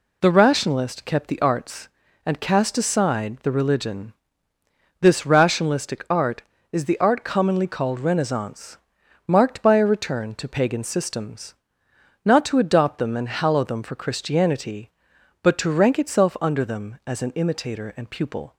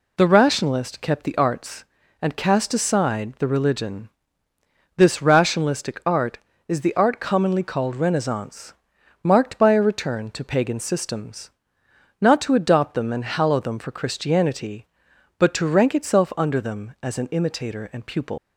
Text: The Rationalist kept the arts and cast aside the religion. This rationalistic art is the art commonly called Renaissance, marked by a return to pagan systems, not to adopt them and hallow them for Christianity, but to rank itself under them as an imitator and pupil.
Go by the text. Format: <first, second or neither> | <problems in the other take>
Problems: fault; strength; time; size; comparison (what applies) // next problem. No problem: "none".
first | leaves "pupil" unfinished; at 18.3 s; 140 ms